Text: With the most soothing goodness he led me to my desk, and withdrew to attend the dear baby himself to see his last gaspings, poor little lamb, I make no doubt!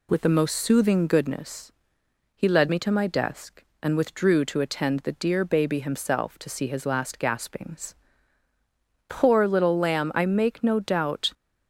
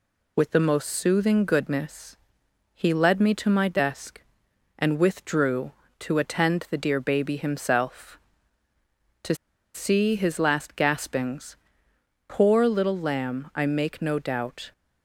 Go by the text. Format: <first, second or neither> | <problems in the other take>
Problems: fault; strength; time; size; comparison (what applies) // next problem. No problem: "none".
first | pauses between "goodness" and "he"; noticeable; at 2.1 s; 0.58 s long; noticeable in the first // pauses between "to" and "see"; at 9.3 s; 0.39 s long